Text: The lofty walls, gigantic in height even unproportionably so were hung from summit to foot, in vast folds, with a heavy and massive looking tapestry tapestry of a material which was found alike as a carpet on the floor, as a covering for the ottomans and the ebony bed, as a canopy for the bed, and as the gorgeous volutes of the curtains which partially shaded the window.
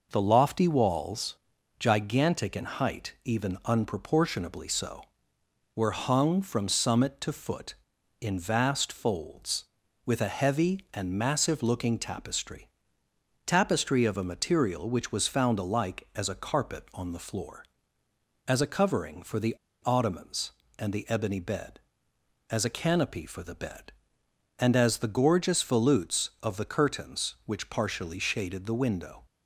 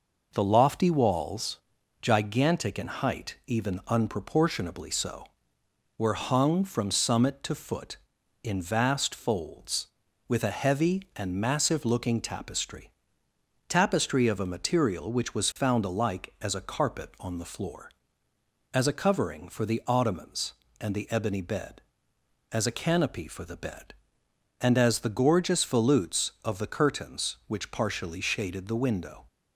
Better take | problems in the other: second | pauses between "tapestry" and "tapestry"; noticeable; at 12.6 s; 0.76 s long; noticeable in the second // pauses between "the" and "ottomans"; slight; at 19.5 s; 0.30 s long

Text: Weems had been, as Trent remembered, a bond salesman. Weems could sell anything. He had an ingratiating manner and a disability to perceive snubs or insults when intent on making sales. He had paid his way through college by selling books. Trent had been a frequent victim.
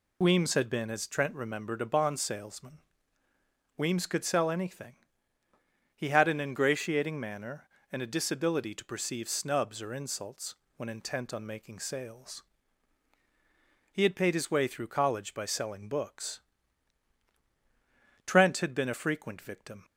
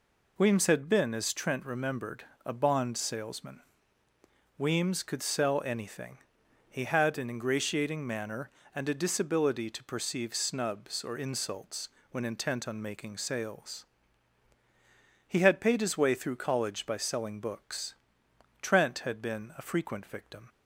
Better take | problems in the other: neither | pauses between "insults" and "when"; slight; the same in both

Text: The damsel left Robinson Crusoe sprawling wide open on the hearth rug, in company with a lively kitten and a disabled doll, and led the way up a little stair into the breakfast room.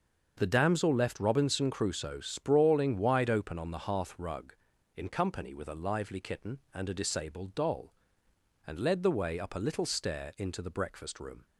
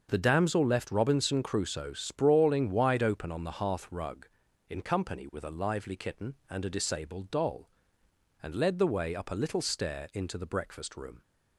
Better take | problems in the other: neither | starts louder than the rest; the same in both

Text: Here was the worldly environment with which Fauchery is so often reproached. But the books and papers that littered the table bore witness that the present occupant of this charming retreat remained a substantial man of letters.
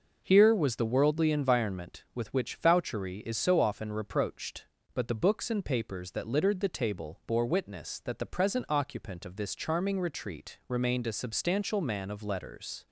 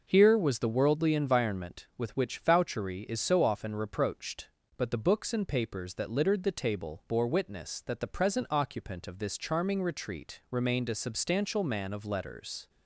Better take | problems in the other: neither | none

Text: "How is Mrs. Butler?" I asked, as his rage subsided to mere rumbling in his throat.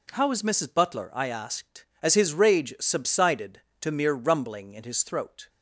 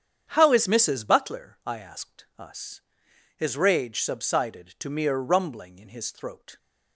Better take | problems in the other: first | starts louder than the rest; strong; until 1.3 s; 8.5 dB // says "us" for "as"; at 2.3 s

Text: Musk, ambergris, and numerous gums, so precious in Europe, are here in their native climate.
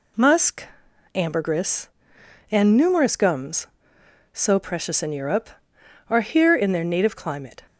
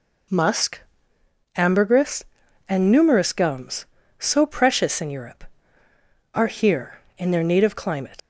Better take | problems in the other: first | leaves "climate" unfinished; at 8.1 s; 140 ms

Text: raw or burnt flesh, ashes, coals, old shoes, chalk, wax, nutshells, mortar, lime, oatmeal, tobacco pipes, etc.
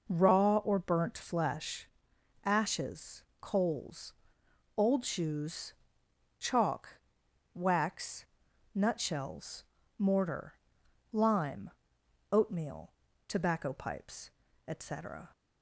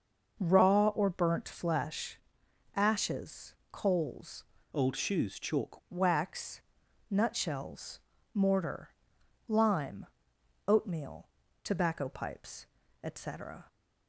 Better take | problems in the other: first | changes voice from "old" to "chalk"; from 4.7 to 5.7 s; 1.0 s long

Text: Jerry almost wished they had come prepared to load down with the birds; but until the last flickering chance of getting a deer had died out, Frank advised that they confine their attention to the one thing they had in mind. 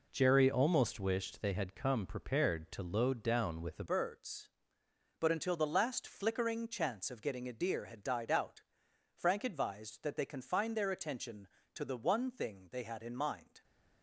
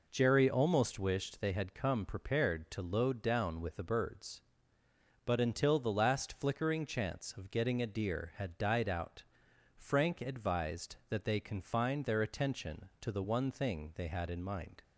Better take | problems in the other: second | changes voice at "birds"; from 3.8 s on; 9.8 s long

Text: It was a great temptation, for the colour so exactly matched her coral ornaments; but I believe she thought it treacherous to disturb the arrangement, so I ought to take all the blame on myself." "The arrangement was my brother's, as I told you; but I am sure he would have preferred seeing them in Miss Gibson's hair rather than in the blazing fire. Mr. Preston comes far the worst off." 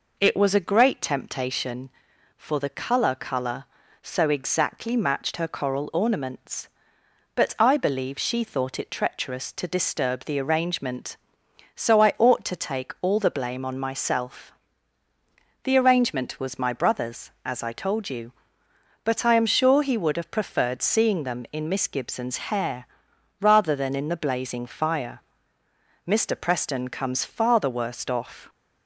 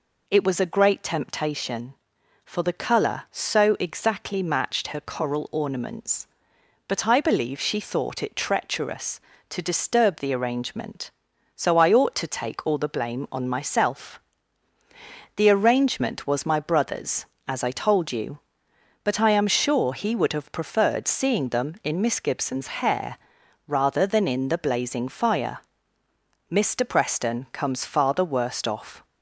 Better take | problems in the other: second | says "colour" twice; at 3.1 s // pauses between "hair" and "rather"; noticeable; at 22.8 s; 0.52 s long; noticeable in the second

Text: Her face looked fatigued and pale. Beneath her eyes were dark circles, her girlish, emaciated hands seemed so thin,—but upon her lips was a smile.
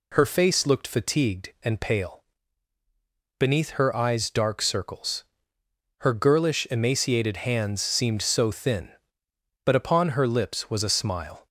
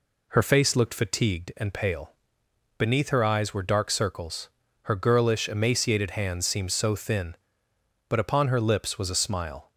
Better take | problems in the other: second | skips "were"; at 4.2 s

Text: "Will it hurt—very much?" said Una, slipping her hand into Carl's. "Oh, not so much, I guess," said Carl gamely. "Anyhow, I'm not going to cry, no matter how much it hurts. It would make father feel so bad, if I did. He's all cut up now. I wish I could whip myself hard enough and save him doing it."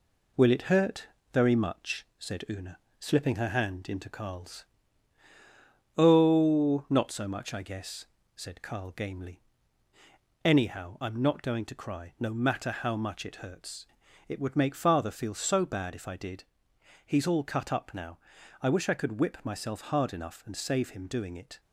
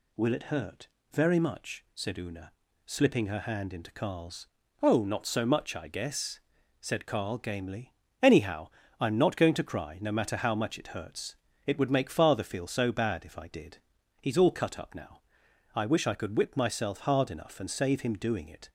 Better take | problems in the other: second | gets quieter; slight; throughout; 3 dB

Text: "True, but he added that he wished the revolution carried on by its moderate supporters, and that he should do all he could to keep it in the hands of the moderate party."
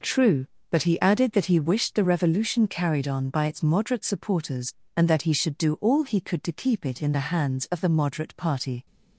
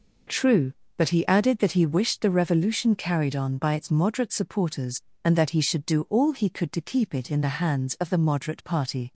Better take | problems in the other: neither | none

